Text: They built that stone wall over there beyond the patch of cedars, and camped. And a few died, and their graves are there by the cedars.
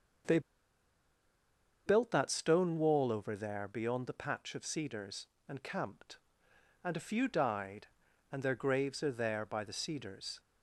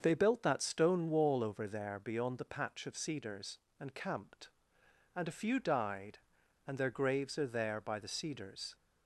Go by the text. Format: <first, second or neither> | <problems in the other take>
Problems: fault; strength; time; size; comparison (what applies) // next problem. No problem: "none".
second | starts louder than the rest; until 2.7 s; 6.5 dB; also in the second // pauses between "They" and "built"; strong; at 0.3 s; 1.4 s long